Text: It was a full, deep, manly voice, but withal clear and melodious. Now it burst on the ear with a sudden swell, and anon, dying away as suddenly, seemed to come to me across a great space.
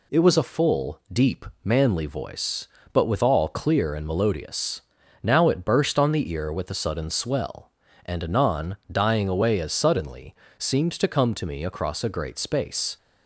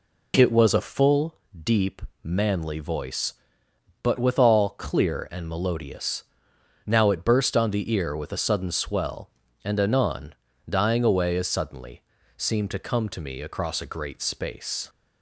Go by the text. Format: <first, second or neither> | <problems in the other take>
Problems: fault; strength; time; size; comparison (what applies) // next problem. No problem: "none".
neither | none